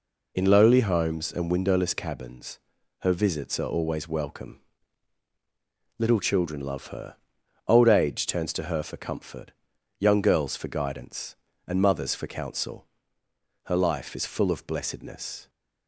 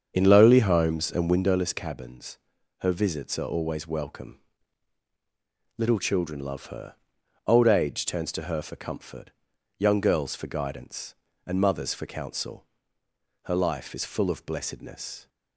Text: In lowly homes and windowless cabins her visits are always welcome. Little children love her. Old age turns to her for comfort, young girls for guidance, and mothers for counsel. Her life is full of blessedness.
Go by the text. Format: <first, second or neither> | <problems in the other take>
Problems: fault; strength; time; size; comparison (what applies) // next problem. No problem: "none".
first | starts louder than the rest; strong; until 1.6 s; 7 dB // pauses between "cabins" and "her"; at 2.3 s; 0.40 s long; also in the first